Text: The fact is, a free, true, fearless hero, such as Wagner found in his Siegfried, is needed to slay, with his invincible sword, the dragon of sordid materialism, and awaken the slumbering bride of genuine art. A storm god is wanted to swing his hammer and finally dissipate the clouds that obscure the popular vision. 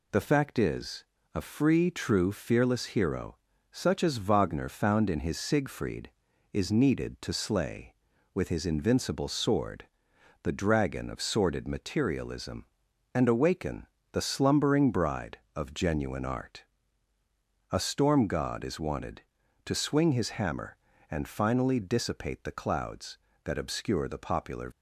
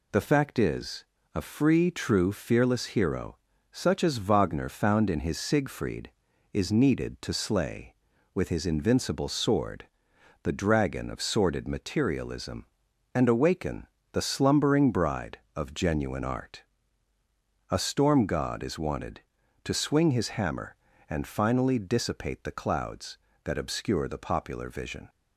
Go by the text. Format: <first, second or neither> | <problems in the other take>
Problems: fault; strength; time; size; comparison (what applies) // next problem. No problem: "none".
second | pauses between "awaken" and "the"; slight; at 13.8 s; 0.26 s long; slight in the second // stops before "vision"; at 24.7 s